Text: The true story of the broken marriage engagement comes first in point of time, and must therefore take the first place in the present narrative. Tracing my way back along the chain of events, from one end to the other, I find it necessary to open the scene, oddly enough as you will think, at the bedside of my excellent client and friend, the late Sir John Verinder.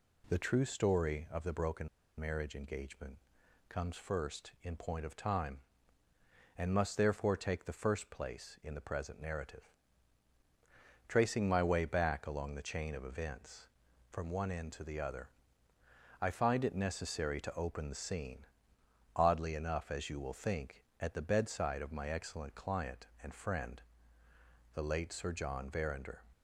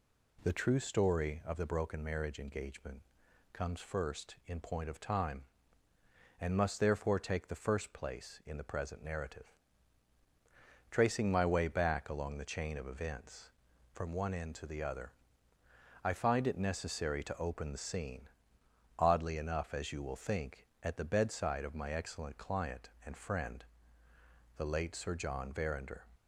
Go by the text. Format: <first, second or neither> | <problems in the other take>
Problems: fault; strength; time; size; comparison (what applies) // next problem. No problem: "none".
second | pauses between "broken" and "marriage"; slight; at 1.8 s; 0.32 s long // pauses between "engagement" and "comes"; noticeable; at 3.1 s; 0.52 s long; noticeable in the second